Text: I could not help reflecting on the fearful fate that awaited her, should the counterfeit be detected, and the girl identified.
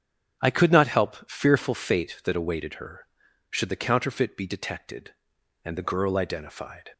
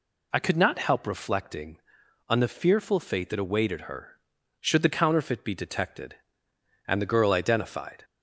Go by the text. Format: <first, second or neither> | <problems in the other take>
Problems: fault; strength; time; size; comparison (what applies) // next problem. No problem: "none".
second | starts louder than the rest; strong; until 1.4 s; 7.5 dB // skips "reflecting on the"; at 1.2 s